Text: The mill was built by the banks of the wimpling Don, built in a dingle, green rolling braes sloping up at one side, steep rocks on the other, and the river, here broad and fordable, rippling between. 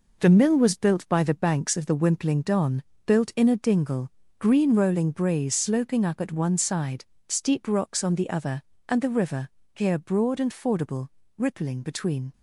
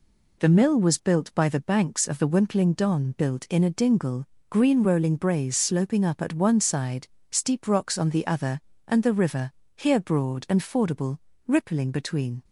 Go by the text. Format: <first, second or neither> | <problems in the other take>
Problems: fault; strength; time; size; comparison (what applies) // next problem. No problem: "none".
second | gets quieter; strong; throughout; 7.5 dB